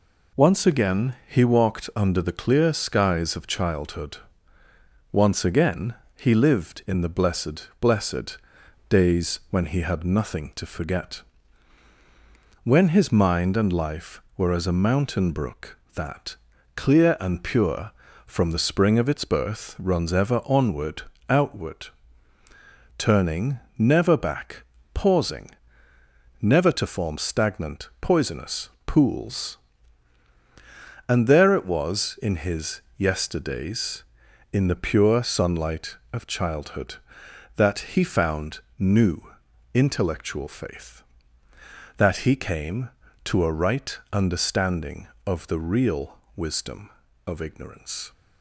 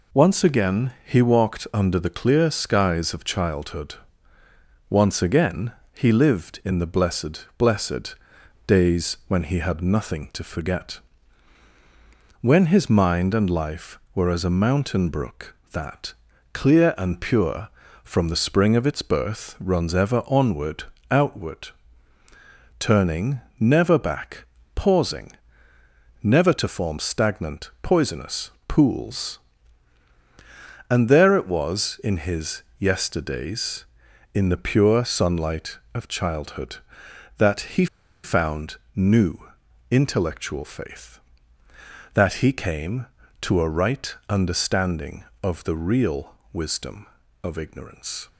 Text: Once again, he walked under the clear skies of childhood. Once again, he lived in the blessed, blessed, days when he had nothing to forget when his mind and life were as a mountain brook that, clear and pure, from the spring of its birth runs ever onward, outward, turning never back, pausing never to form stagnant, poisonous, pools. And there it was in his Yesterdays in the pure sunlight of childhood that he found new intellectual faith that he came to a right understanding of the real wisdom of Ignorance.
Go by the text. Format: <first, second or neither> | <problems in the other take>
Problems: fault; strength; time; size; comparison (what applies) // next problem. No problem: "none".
first | pauses between "forget" and "when"; strong; at 10.9 s; 1.4 s long; strong in the first // pauses between "turning" and "never"; slight; at 23.3 s; 0.20 s long; slight in the first // pauses between "pausing" and "never"; noticeable; at 25.3 s; 0.92 s long; noticeable in the first // pauses between "his" and "Yesterdays"; slight; at 32.6 s; 0.16 s long; slight in the first // pauses between "he" and "found"; at 37.8 s; 0.38 s long // pauses between "found" and "new"; slight; at 38.7 s; 0.20 s long; slight in the first // pauses between "new" and "intellectual"; noticeable; at 39.3 s; 0.50 s long; noticeable in the first // pauses between "real" and "wisdom"; slight; at 46.3 s; 0.18 s long; slight in the first